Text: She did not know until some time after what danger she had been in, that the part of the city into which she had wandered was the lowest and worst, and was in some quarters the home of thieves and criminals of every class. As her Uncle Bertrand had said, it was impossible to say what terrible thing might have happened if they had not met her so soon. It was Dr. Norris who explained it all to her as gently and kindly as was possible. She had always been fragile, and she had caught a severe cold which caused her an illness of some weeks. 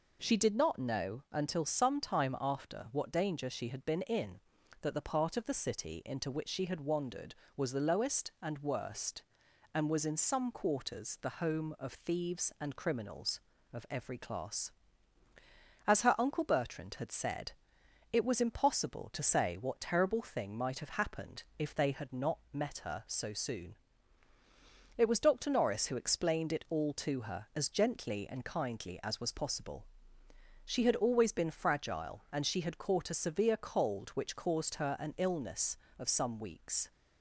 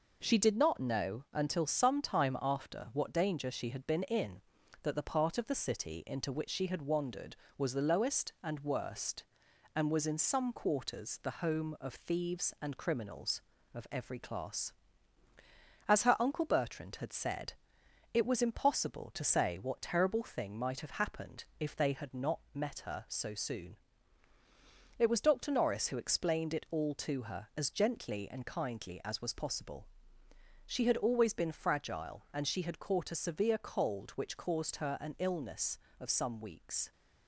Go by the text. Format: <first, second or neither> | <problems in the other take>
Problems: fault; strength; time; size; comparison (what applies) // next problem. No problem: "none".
first | gets quieter; throughout; 4 dB // pauses between "not" and "met"; slight; at 22.3 s; 0.16 s long; slight in the first